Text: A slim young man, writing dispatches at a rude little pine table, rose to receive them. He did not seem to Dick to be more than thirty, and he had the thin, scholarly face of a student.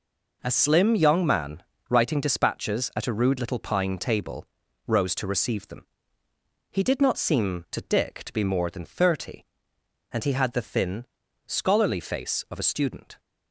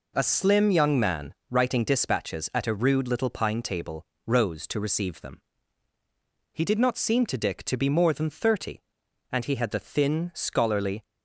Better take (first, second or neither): first